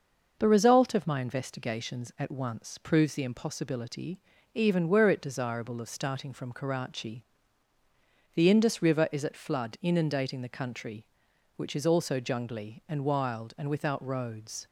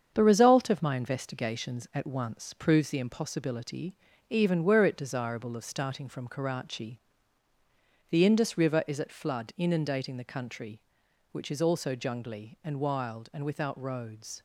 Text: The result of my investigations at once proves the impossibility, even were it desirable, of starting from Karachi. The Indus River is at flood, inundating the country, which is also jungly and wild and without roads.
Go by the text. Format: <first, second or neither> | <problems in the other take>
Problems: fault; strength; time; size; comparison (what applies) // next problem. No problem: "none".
first | gets quieter; noticeable; throughout; 6 dB // starts louder than the rest; strong; until 1.1 s; 7.5 dB; noticeable in the first